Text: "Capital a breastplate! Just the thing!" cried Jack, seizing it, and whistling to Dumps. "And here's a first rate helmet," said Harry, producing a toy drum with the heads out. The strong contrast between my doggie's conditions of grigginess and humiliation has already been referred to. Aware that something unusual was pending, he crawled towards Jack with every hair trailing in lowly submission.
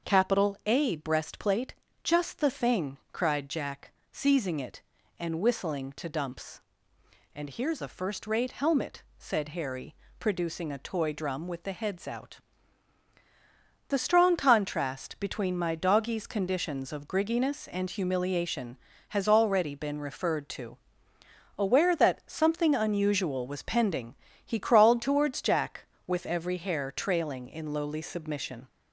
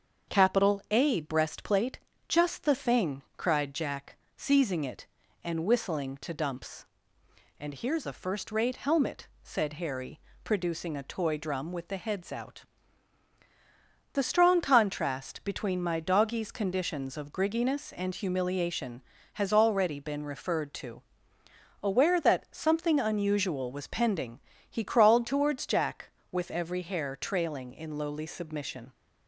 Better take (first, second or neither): second